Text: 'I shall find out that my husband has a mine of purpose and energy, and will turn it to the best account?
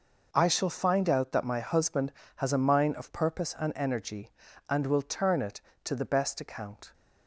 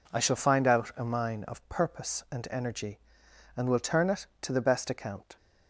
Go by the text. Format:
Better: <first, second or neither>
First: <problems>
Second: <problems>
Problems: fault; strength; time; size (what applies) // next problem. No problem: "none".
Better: first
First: none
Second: skips "that my husband has"; at 0.9 s